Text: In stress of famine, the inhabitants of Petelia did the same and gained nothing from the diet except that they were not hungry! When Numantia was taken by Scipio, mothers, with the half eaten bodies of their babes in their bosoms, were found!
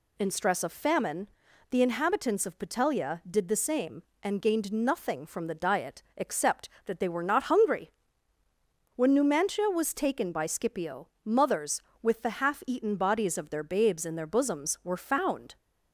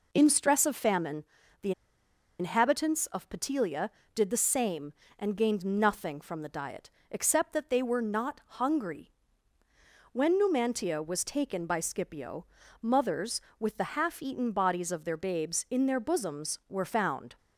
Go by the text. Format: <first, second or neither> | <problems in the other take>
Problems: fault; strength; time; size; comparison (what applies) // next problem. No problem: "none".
first | pauses between "the" and "inhabitants"; noticeable; at 1.7 s; 0.68 s long // pauses between "diet" and "except"; slight; at 6.9 s; 0.20 s long